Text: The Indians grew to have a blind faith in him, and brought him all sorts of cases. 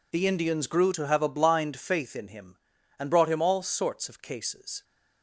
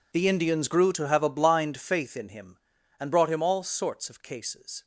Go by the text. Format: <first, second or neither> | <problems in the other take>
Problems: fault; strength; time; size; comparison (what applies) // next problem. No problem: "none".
first | gets quieter; strong; throughout; 18 dB